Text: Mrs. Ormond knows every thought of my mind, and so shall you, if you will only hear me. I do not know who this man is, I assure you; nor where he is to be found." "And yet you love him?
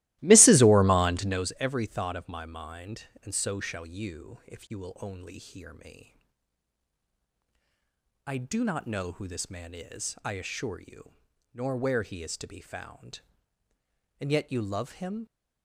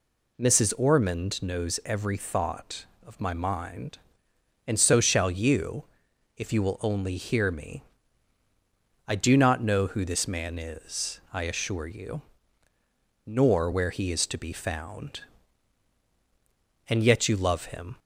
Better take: second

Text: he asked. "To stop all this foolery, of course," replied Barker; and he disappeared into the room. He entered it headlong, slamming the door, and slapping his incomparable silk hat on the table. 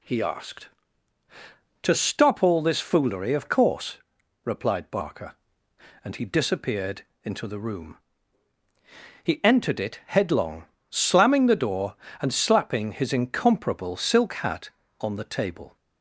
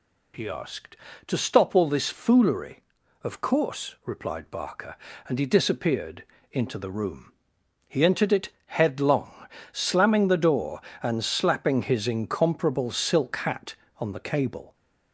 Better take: first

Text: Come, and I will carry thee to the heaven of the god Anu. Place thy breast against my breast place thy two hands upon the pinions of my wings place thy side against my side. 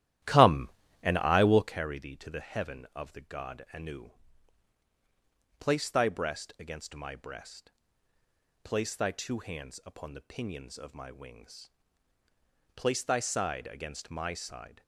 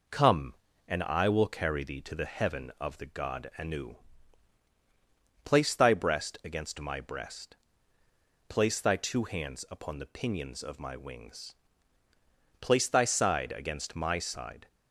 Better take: second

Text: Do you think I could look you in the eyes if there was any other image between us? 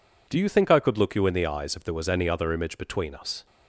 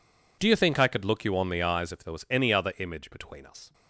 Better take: first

